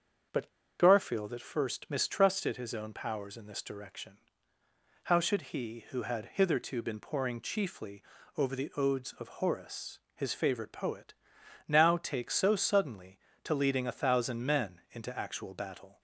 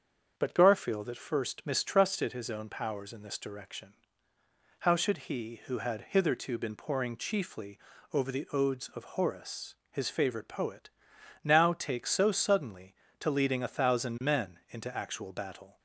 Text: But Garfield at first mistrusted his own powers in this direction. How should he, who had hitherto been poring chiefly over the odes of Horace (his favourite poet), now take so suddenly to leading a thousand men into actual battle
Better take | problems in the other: second | starts louder than the rest; strong; until 1.6 s; 7 dB; strong in the second // pauses between "But" and "Garfield"; slight; at 0.4 s; 0.32 s long // pauses between "chiefly" and "over"; slight; at 8.0 s; 0.34 s long; slight in the second

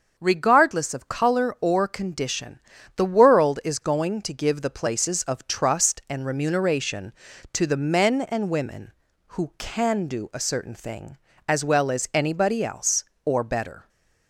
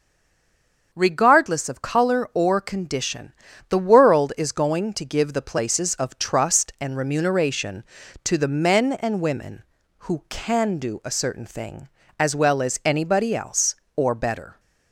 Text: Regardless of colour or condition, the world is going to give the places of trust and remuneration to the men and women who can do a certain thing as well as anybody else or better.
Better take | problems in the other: first | stays silent before the first word; slight; until 0.9 s; 0.9 s long // starts louder than the rest; until 1.9 s; 6.5 dB; also in the first

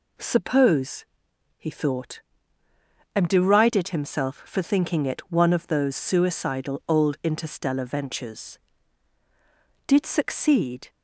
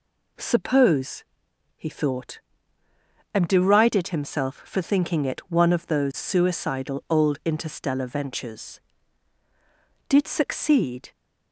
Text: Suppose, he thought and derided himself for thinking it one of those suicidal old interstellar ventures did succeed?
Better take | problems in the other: neither | none

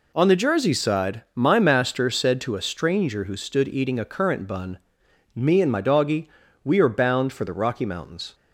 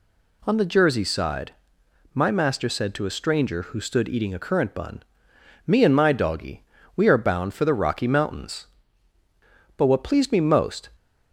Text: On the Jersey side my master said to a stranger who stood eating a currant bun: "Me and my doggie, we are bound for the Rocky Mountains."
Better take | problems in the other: first | pauses between "side" and "my"; noticeable; at 1.5 s; 0.62 s long // goes on to say "But what pleased me most"; noticeable; from 9.7 s on; 1.1 s long

